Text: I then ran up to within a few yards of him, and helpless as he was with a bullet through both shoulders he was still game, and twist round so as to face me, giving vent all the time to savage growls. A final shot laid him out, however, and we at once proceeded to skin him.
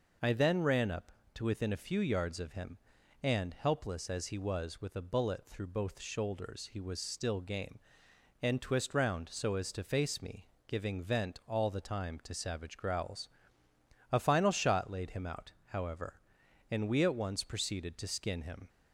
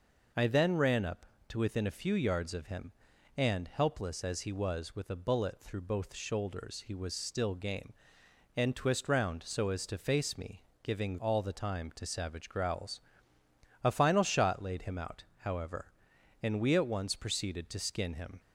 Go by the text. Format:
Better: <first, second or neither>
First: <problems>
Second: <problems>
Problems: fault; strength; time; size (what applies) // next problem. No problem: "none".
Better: first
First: none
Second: skips "vent"; at 11.1 s